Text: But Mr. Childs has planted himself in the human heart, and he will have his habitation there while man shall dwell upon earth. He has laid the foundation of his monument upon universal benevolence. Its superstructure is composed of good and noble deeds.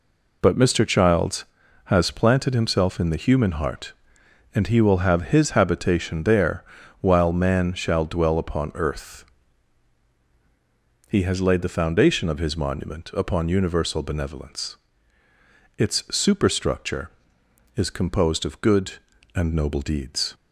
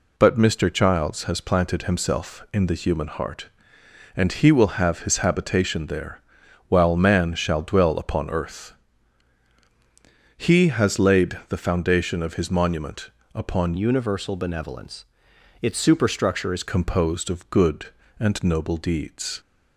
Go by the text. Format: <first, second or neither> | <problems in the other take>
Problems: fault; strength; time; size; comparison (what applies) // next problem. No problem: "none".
first | pauses between "there" and "while"; noticeable; at 6.2 s; 0.48 s long; also in the first // pauses between "monument" and "upon"; slight; at 13.1 s; 0.24 s long // changes voice from "universal" to "is"; from 13.7 to 16.6 s; 2.9 s long